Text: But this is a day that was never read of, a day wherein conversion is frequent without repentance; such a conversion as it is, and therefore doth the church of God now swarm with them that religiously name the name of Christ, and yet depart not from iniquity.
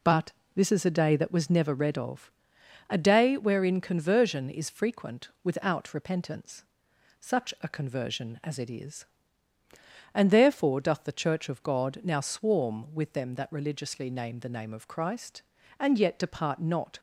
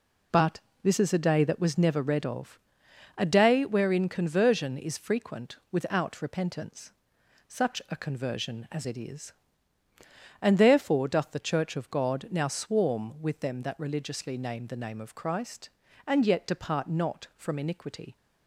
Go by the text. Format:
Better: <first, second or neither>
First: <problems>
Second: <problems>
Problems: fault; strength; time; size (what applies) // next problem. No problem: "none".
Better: second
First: pauses between "But" and "this"; slight; at 0.3 s; 0.22 s long // stops before "from iniquity"; at 16.9 s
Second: pauses between "But" and "this"; slight; at 0.5 s; 0.22 s long